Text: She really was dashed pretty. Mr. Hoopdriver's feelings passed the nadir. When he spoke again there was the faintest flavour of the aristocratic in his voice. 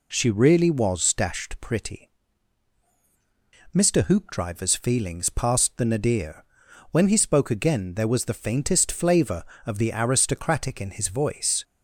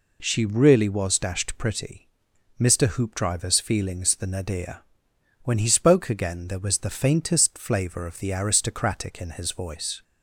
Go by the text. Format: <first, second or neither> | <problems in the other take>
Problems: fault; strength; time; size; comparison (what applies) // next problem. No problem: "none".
first | skips "passed"; at 4.1 s